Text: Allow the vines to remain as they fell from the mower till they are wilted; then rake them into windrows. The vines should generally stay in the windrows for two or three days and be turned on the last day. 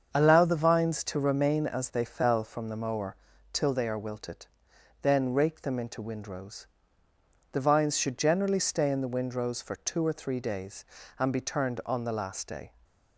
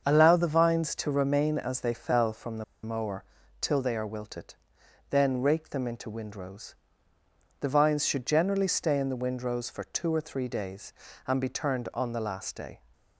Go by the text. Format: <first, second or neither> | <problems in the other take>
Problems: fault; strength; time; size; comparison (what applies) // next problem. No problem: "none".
first | starts louder than the rest; until 1.0 s; 7 dB; also in the first // pauses between "the" and "mower"; slight; at 2.6 s; 0.19 s long // pauses between "mower" and "till"; slight; at 3.2 s; 0.36 s long; slight in the first